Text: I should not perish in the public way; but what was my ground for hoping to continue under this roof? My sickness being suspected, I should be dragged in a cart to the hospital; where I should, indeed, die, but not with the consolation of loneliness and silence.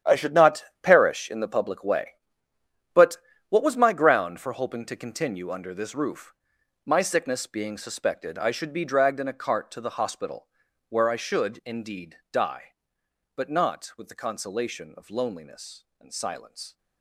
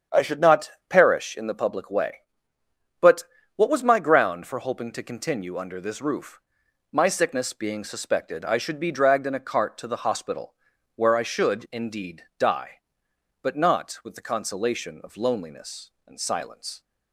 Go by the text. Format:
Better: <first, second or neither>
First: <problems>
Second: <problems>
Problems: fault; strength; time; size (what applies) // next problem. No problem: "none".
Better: second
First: gets quieter; strong; throughout; 14 dB // starts louder than the rest; strong; until 1.2 s; 10 dB // pauses between "not" and "perish"; slight; at 0.6 s; 0.18 s long // pauses between "but" and "what"; slight; at 3.1 s; 0.32 s long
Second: starts louder than the rest; strong; until 1.3 s; 8 dB // pauses between "not" and "perish"; slight; at 0.6 s; 0.18 s long // pauses between "but" and "what"; slight; at 3.2 s; 0.32 s long